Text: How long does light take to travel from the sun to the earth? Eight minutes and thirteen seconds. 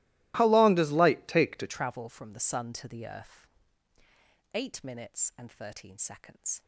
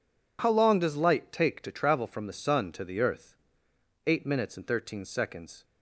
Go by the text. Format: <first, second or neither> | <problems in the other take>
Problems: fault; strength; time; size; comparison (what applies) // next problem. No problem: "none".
second | starts louder than the rest; strong; until 1.3 s; 18.5 dB // changes voice at "travel"; from 1.6 s on; 5.0 s long